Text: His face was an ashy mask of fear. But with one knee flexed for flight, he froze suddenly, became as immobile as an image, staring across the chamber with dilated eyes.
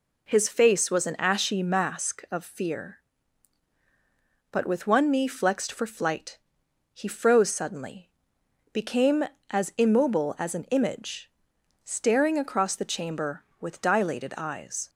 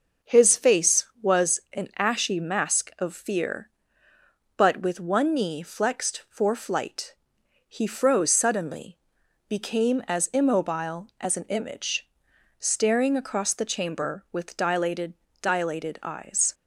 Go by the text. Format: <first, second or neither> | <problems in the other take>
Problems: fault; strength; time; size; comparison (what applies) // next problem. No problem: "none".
first | says "dilated" twice; at 15.4 s